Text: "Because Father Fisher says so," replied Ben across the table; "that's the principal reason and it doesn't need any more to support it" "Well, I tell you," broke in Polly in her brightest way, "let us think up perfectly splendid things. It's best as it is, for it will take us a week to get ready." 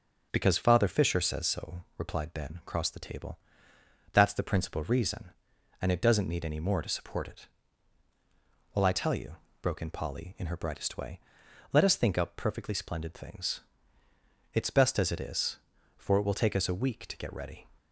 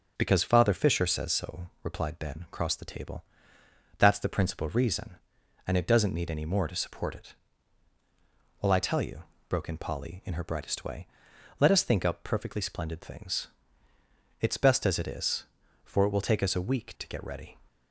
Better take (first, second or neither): neither